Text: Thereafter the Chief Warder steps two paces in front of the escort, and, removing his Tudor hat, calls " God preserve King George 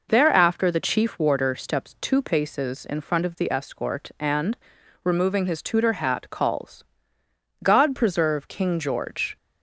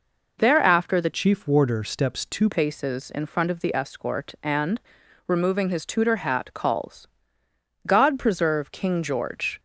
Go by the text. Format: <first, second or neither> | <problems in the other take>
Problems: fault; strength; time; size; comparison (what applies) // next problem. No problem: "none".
first | changes voice from "Chief" to "two"; from 1.1 to 2.4 s; 1.3 s long